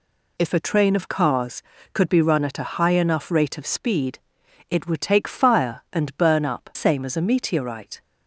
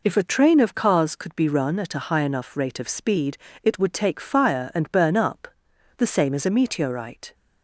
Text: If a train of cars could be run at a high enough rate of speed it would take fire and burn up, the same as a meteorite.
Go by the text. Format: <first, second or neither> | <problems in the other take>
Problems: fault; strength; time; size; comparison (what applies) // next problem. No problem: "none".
second | pauses between "speed" and "it"; noticeable; at 4.1 s; 0.50 s long; slight in the second // skips "the"; at 6.7 s